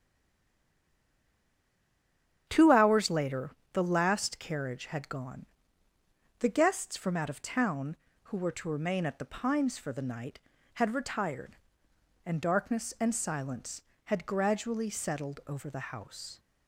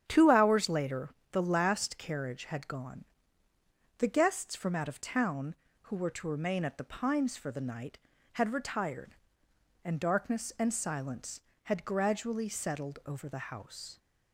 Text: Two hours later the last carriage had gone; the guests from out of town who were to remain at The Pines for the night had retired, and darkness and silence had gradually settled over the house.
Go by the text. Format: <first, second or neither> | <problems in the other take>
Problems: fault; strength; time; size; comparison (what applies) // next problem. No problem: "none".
second | stays silent before the first word; until 2.4 s; 2.4 s long // starts louder than the rest; strong; until 3.5 s; 9 dB; strong in the second // pauses between "later" and "the"; slight; at 3.5 s; 0.22 s long; slight in the second